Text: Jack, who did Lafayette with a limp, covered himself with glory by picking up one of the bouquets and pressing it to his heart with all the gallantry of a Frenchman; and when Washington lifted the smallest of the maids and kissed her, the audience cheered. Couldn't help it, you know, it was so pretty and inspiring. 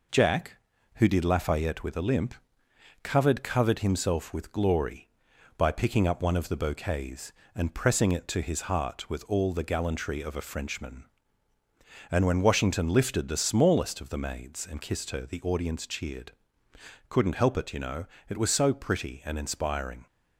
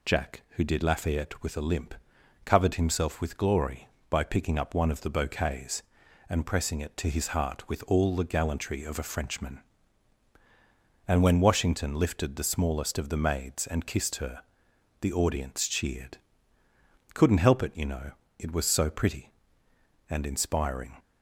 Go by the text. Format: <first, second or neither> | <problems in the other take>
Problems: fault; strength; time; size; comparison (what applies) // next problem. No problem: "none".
second | says "covered" twice; at 3.4 s